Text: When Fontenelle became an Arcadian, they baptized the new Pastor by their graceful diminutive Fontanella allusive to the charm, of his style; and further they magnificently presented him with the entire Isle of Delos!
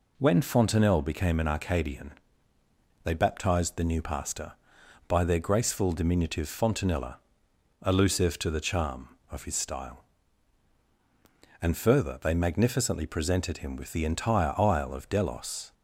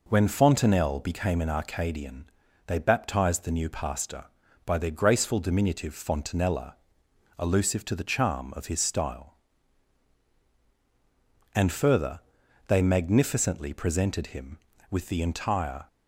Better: first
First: pauses between "Fontanella" and "allusive"; noticeable; at 7.1 s; 0.66 s long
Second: pauses between "Fontanella" and "allusive"; noticeable; at 6.7 s; 0.62 s long // pauses between "further" and "they"; noticeable; at 12.2 s; 0.48 s long // stops before "Isle of Delos"; at 15.8 s

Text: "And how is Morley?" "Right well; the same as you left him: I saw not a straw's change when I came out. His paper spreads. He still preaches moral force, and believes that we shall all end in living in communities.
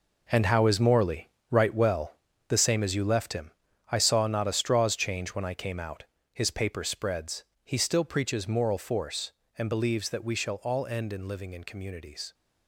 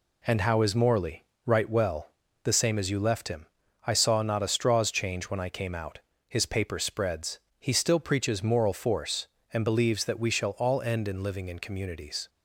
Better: second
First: gets quieter; strong; throughout; 11.5 dB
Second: none

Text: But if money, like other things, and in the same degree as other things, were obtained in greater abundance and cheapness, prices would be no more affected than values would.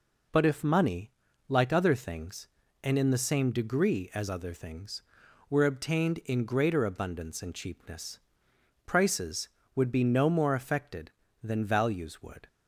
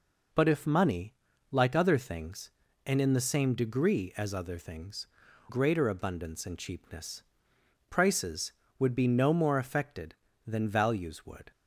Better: first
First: none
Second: skips "were obtained in"; at 5.2 s

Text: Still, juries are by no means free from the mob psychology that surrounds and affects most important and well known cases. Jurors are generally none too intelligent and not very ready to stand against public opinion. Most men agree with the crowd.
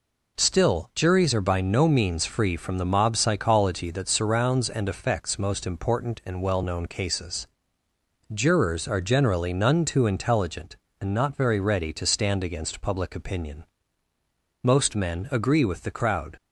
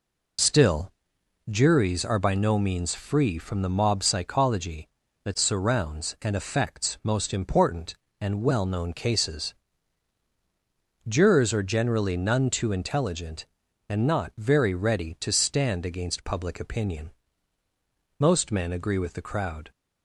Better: first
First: none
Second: loses the start of "Still"; at 0.3 s; 50 ms

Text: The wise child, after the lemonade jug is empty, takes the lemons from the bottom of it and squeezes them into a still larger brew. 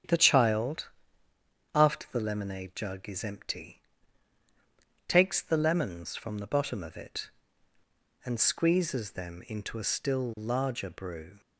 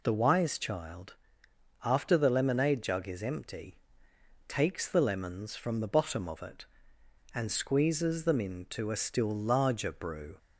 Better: second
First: starts louder than the rest; strong; until 1.9 s; 9 dB // skips "wise"; at 0.1 s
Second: none

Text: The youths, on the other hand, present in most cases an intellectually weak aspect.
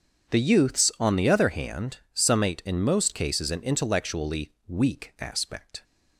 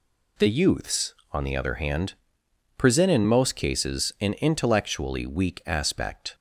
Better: second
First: starts louder than the rest; strong; until 1.3 s; 7.5 dB // says "summate" for "present"; at 2.1 s // pauses between "intellectually" and "weak"; slight; at 4.5 s; 0.16 s long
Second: none

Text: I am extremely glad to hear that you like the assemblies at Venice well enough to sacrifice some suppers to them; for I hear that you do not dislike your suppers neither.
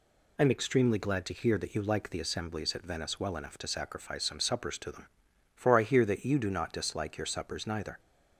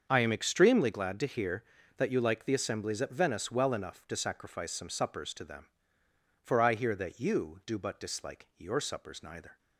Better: first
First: none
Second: starts louder than the rest; until 1.1 s; 7 dB // says "but" for "not"; at 7.7 s

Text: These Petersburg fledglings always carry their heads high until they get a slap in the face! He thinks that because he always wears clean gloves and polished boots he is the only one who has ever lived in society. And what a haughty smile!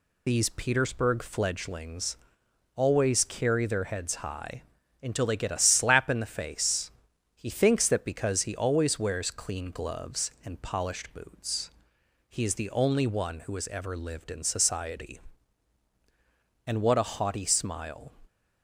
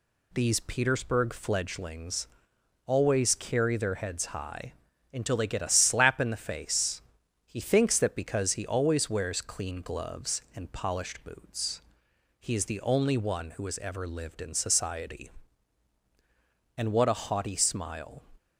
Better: second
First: loses the start of "These"; at 0.2 s; 60 ms // pauses between "fledglings" and "always"; noticeable; at 2.1 s; 0.60 s long // pauses between "high" and "until"; at 4.6 s; 0.40 s long // pauses between "boots" and "he"; noticeable; at 11.7 s; 0.58 s long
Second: pauses between "fledglings" and "always"; noticeable; at 2.2 s; 0.60 s long // pauses between "high" and "until"; at 4.7 s; 0.40 s long // pauses between "boots" and "he"; noticeable; at 11.8 s; 0.58 s long

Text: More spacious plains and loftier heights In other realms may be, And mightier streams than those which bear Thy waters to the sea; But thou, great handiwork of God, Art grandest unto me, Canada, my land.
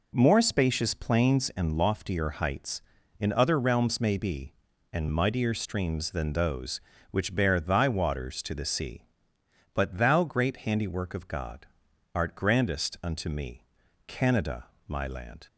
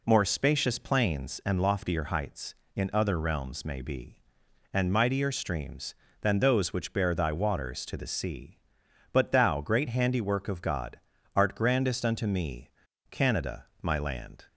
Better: neither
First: none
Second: none

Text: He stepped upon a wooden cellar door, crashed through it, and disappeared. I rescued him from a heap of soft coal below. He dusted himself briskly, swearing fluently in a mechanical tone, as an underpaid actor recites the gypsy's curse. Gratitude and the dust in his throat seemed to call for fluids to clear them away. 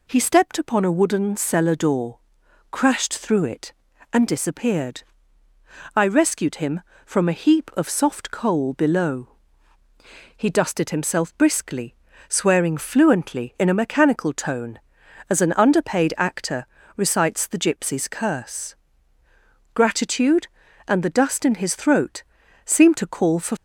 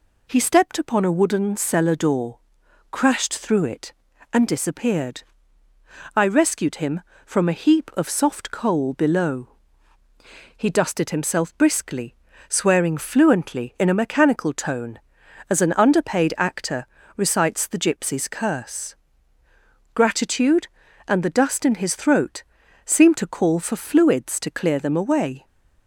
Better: second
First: pauses between "actor" and "recites"; slight; at 16.6 s; 0.30 s long // pauses between "throat" and "seemed"; at 22.2 s; 0.42 s long // stops before "fluids to clear them away"; at 23.5 s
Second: pauses between "actor" and "recites"; slight; at 16.8 s; 0.30 s long // pauses between "throat" and "seemed"; at 22.4 s; 0.42 s long

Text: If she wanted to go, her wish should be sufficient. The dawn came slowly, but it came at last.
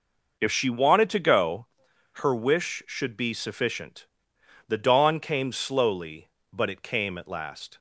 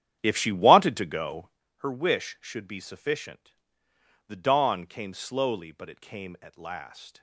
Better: first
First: none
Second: starts louder than the rest; strong; until 1.7 s; 10 dB

